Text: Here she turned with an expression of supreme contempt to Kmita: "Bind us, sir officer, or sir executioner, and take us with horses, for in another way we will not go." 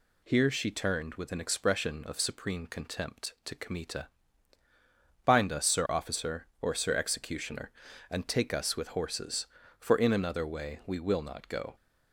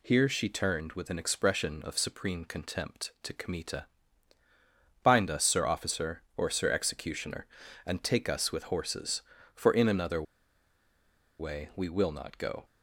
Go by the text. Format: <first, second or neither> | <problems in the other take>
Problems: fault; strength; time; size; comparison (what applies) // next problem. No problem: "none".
first | pauses between "another" and "way"; at 10.2 s; 1.1 s long